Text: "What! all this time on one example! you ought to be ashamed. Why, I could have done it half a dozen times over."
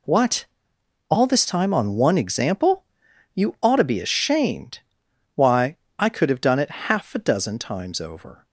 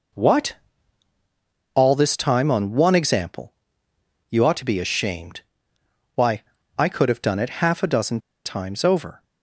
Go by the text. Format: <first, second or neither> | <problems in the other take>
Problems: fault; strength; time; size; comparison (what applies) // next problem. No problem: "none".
first | pauses between "dozen" and "times"; slight; at 8.1 s; 0.26 s long